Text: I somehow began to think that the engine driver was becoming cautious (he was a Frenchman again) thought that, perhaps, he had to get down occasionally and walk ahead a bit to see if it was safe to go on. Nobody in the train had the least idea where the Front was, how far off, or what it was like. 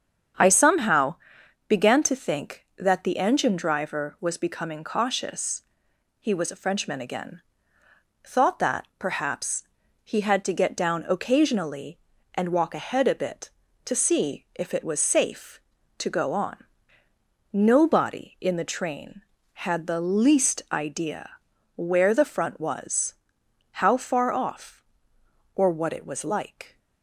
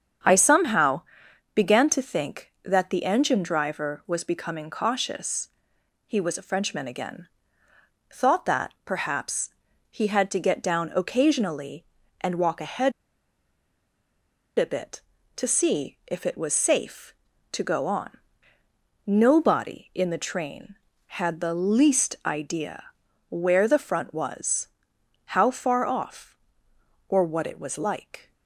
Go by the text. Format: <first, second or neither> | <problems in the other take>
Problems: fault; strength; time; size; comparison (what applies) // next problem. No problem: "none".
first | starts louder than the rest; strong; until 1.7 s; 8 dB; strong in the first // pauses between "somehow" and "began"; noticeable; at 1.0 s; 0.54 s long; noticeable in the first // pauses between "ahead" and "a"; strong; at 12.9 s; 1.6 s long // pauses between "idea" and "where"; noticeable; at 22.8 s; 0.48 s long; noticeable in the first